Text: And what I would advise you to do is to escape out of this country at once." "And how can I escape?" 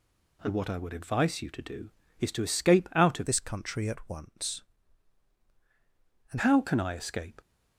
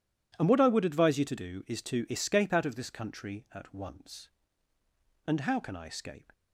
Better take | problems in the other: second | changes voice from "this" to "And"; from 3.2 to 6.3 s; 3.1 s long

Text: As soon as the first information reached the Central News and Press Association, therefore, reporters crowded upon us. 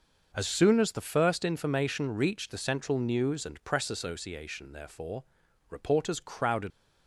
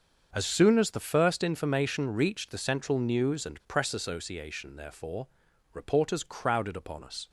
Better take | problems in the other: second | starts louder than the rest; noticeable; until 1.3 s; 6 dB; also in the second // stops before "upon us"; at 6.7 s

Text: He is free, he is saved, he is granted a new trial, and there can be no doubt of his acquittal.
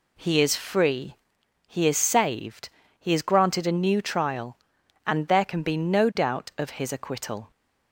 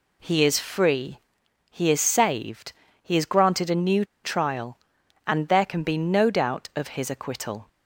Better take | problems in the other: first | pauses between "new" and "trial"; slight; at 4.0 s; 0.19 s long

